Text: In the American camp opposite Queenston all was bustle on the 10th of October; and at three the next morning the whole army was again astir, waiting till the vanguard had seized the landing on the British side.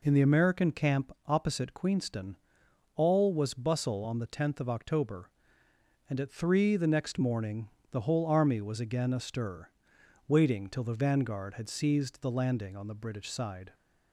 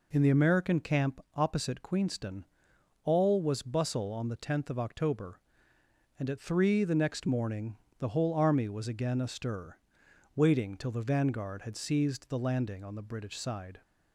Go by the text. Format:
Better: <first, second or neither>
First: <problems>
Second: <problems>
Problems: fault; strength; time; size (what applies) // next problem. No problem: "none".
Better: neither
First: pauses between "Queenston" and "all"; noticeable; at 2.3 s; 0.60 s long // pauses between "morning" and "the"; slight; at 7.6 s; 0.24 s long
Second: pauses between "Queenston" and "all"; noticeable; at 2.4 s; 0.60 s long // pauses between "morning" and "the"; slight; at 7.7 s; 0.24 s long